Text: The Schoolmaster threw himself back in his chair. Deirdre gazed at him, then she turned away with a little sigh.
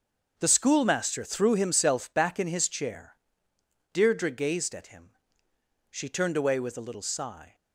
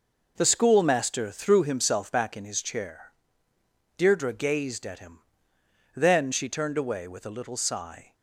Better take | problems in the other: second | starts louder than the rest; until 1.3 s; 6.5 dB // skips "then"; at 5.5 s

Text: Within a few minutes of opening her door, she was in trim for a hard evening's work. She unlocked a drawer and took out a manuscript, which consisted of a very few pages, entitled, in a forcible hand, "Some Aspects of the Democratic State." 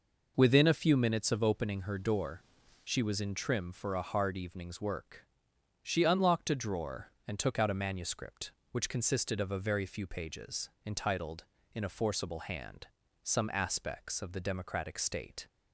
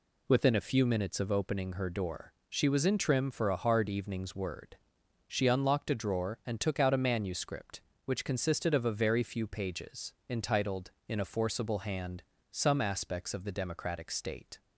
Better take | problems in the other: first | says "word" for "work"; at 4.3 s

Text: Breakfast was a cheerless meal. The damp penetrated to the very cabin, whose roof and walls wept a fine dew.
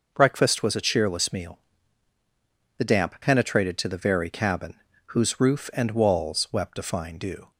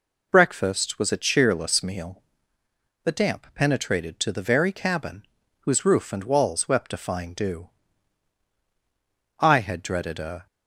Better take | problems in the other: first | goes on to say "I had dreaded a"; noticeable; from 9.4 s on; 1.0 s long

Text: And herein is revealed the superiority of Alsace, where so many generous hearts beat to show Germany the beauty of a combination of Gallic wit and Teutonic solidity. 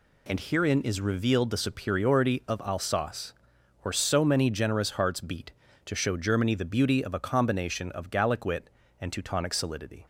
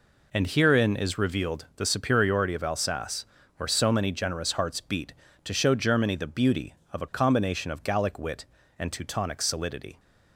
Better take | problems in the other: neither | none

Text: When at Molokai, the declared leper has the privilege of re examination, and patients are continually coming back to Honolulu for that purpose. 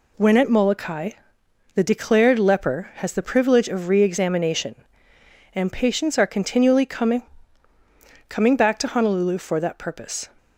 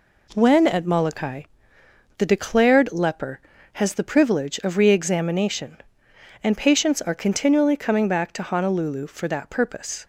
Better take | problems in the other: second | says "coming" twice; at 8.2 s

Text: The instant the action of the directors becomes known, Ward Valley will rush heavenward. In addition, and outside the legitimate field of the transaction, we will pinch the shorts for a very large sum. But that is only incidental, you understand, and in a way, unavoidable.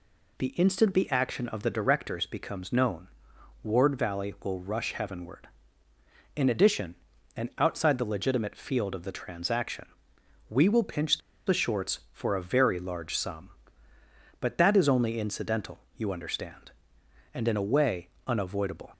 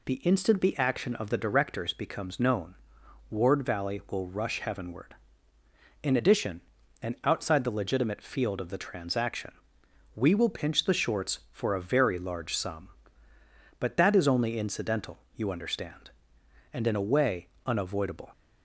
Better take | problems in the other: second | pauses between "pinch" and "the"; slight; at 11.2 s; 0.26 s long

